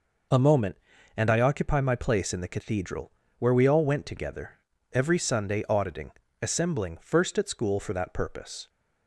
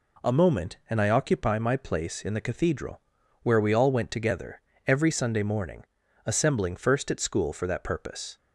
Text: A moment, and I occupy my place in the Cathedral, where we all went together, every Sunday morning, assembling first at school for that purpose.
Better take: second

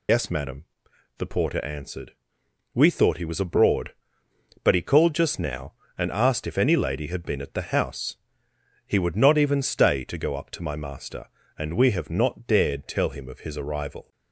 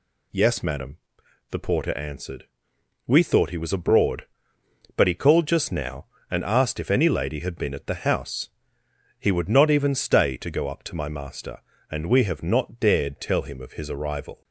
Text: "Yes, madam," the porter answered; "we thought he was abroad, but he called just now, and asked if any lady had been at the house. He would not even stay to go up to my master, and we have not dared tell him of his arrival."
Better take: second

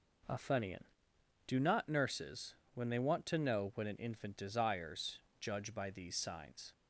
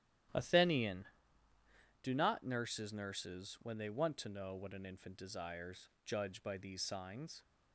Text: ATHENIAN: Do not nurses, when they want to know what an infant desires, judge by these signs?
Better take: first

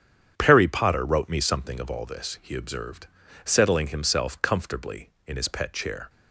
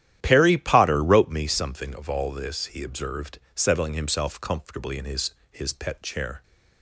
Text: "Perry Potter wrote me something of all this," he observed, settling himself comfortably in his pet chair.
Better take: first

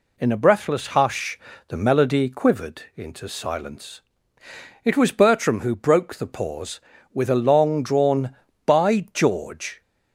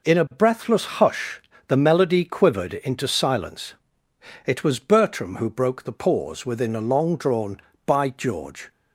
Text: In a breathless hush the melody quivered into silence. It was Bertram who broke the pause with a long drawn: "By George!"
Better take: first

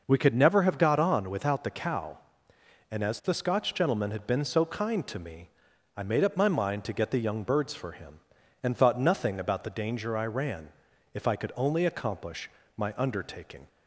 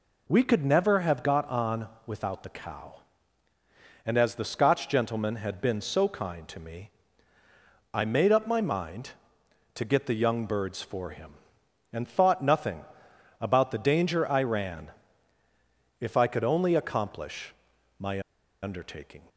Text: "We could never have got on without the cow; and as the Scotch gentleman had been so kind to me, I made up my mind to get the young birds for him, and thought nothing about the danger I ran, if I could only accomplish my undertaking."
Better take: first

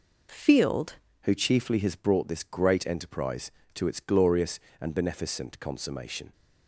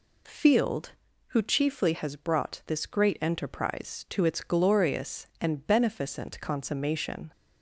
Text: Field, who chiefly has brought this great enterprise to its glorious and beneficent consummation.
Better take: second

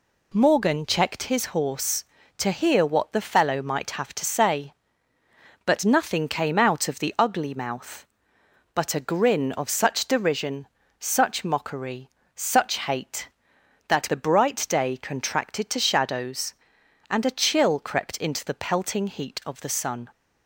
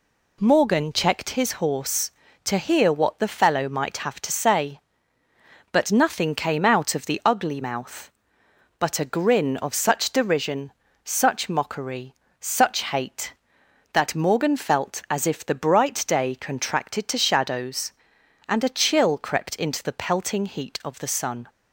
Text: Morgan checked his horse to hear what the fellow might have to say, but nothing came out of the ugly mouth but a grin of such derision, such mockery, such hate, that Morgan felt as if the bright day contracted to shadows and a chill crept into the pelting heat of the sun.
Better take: second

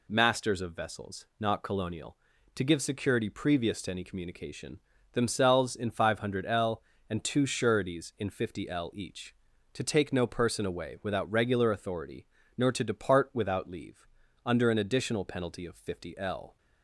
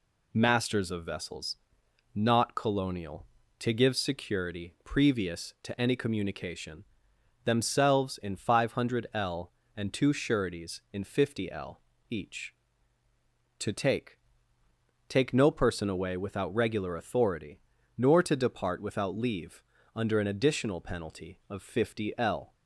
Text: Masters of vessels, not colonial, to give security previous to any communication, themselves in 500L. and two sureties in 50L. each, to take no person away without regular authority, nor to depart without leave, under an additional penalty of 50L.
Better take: first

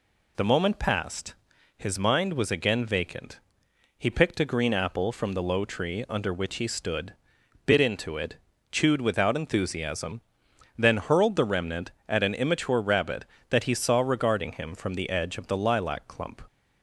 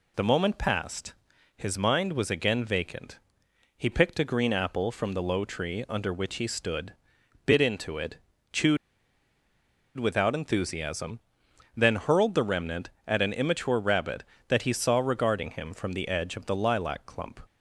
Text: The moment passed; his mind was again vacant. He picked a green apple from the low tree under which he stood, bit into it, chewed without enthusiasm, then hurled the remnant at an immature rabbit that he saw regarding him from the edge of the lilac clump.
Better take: first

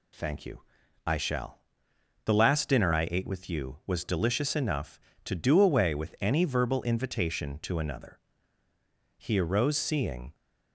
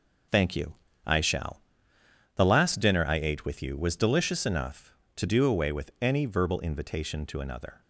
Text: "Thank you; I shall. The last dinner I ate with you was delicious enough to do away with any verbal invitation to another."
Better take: second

